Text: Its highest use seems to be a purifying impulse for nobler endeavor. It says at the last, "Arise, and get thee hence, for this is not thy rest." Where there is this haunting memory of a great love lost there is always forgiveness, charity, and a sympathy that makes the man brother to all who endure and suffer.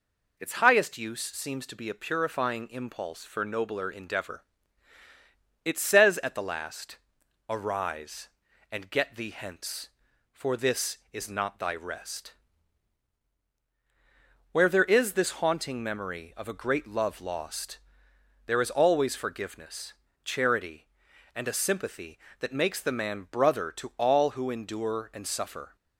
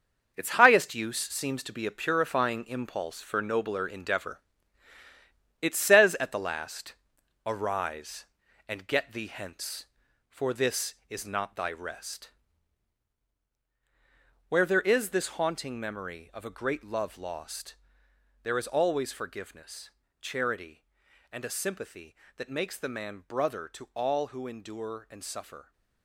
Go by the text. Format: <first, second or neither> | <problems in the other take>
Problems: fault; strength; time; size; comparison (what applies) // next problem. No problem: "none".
first | gets quieter; strong; throughout; 9 dB // pauses between "lost" and "there"; noticeable; at 17.7 s; 0.66 s long; noticeable in the first